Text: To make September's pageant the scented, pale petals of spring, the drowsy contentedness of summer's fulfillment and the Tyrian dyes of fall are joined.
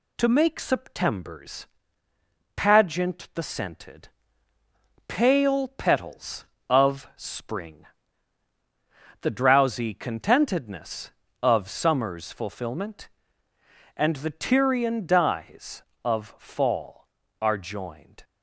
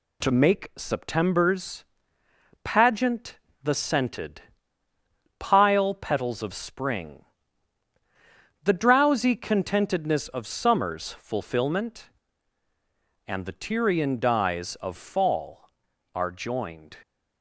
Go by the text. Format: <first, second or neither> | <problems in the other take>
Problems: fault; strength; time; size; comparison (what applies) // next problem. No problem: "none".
first | pauses between "September's" and "pageant"; noticeable; at 1.8 s; 0.78 s long; noticeable in the first // pauses between "pageant" and "the"; slight; at 3.3 s; 0.24 s long // says "pile" for "pale"; at 5.3 s